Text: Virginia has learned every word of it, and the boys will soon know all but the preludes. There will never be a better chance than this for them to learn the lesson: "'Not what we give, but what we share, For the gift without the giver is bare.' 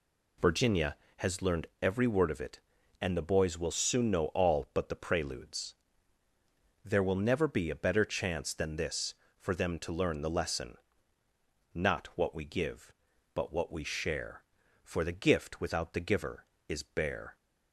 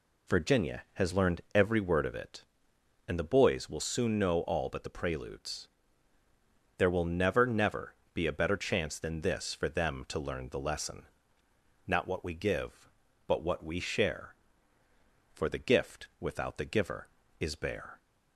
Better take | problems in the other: first | says "never" twice; at 7.4 s

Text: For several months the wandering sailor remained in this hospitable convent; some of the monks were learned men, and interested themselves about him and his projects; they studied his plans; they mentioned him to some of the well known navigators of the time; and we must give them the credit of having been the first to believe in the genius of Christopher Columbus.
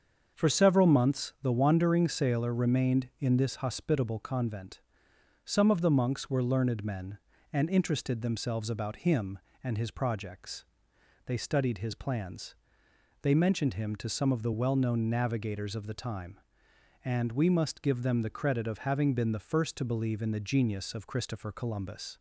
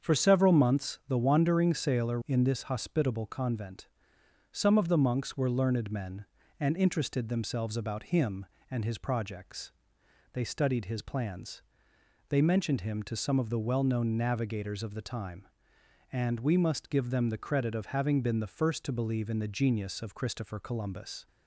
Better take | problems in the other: first | starts louder than the rest; strong; until 1.1 s; 7 dB; also in the first // skips "remained"; at 2.2 s

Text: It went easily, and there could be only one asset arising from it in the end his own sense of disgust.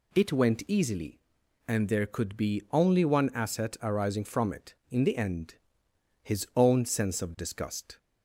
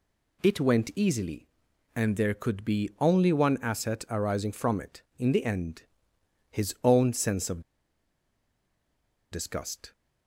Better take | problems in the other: first | pauses between "end" and "his"; noticeable; at 5.8 s; 0.68 s long; noticeable in the first // pauses between "of" and "disgust"; strong; at 7.6 s; 1.7 s long

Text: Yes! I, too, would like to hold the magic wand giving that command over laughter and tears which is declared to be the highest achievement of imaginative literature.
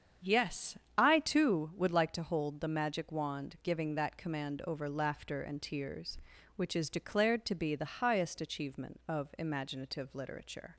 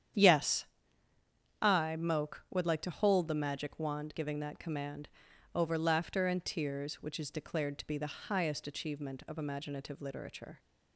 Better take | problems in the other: first | starts louder than the rest; strong; until 2.1 s; 9 dB; strong in the first // says "moke" for "too"; at 1.9 s // pauses between "command" and "over"; at 5.0 s; 0.44 s long

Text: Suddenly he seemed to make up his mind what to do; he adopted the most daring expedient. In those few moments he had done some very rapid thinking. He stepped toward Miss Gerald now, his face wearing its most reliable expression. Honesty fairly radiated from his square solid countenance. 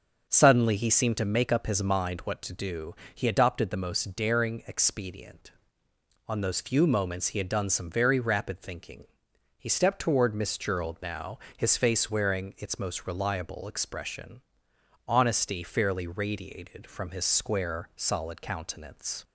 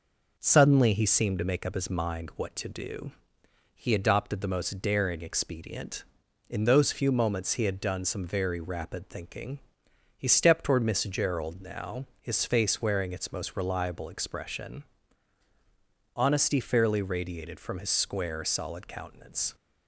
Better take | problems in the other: second | starts louder than the rest; until 1.3 s; 6.5 dB // says "On" for "In"; at 6.2 s

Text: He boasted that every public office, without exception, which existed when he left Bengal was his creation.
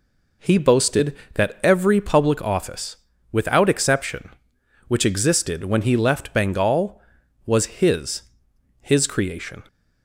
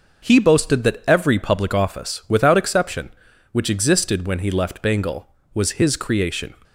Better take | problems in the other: second | says "his" twice; at 8.7 s

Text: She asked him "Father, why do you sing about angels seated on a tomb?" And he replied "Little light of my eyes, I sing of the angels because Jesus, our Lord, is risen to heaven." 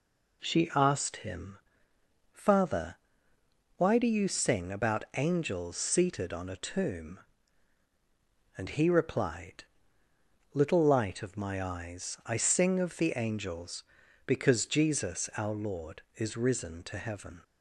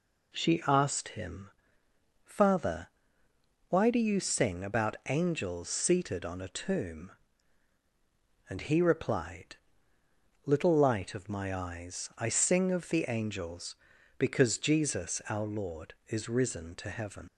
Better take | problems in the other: first | pauses between "him" and "Father"; noticeable; at 1.5 s; 0.74 s long; noticeable in the first // pauses between "replied" and "Little"; noticeable; at 9.5 s; 0.90 s long; noticeable in the first // leaves "heaven" unfinished; at 17.2 s; 65 ms

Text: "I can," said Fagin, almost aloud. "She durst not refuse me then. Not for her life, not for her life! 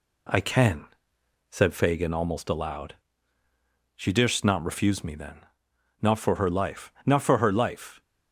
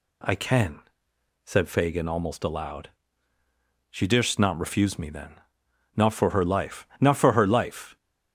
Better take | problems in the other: second | gets quieter; slight; throughout; 2 dB

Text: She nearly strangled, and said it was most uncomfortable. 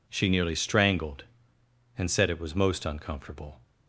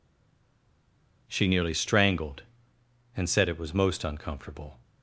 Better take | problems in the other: first | stays silent before the first word; noticeable; until 1.2 s; 1.2 s long

